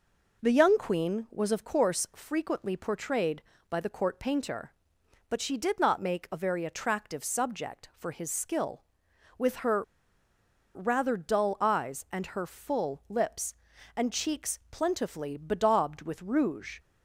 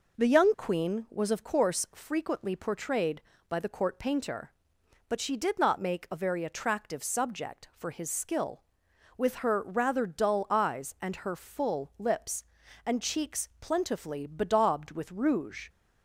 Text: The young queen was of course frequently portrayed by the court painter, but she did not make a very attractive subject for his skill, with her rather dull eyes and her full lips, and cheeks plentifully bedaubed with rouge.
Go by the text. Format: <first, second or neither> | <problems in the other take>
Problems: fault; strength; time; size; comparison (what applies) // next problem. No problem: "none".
second | pauses between "her" and "rather"; noticeable; at 9.8 s; 0.91 s long